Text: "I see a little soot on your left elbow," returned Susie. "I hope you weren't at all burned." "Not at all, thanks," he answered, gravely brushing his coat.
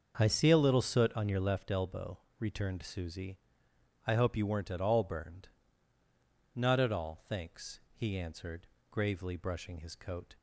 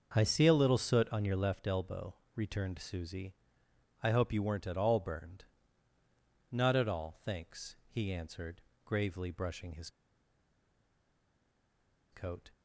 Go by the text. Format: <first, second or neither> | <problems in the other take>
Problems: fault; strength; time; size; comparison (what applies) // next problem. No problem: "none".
first | starts louder than the rest; until 1.1 s; 6.5 dB; also in the first // pauses between "his" and "coat"; strong; at 9.8 s; 2.2 s long